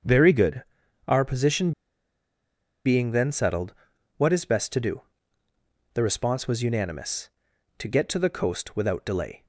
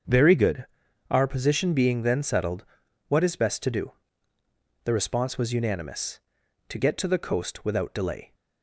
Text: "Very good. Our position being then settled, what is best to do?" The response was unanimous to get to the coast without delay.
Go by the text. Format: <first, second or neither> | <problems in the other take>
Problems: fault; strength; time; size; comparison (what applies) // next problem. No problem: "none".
second | starts louder than the rest; until 1.5 s; 7 dB; also in the second // pauses between "position" and "being"; at 1.7 s; 1.1 s long